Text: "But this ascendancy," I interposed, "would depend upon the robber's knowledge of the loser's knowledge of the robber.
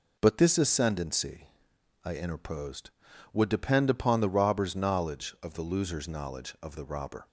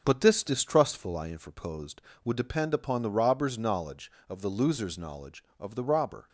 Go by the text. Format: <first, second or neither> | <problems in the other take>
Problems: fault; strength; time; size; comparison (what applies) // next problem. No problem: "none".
first | starts louder than the rest; until 1.0 s; 6.5 dB // says "distrustful" for "ascendancy"; at 0.4 s